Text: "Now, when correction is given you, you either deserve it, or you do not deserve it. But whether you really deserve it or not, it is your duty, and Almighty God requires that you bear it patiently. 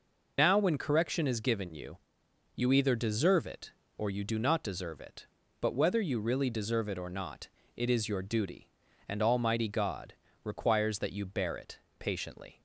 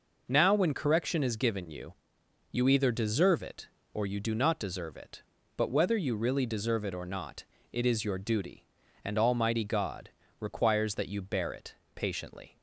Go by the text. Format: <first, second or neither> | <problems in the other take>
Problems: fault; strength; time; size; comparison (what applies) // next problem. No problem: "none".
second | loses the start of "Now"; at 0.3 s; 55 ms // pauses between "God" and "requires"; slight; at 10.1 s; 0.28 s long; slight in the second // pauses between "it" and "patiently"; slight; at 11.7 s; 0.20 s long; slight in the second